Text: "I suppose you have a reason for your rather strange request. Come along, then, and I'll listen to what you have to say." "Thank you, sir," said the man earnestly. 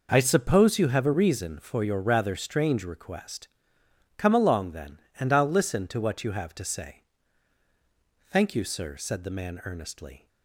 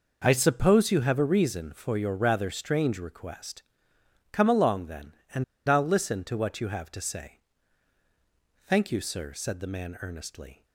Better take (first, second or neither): first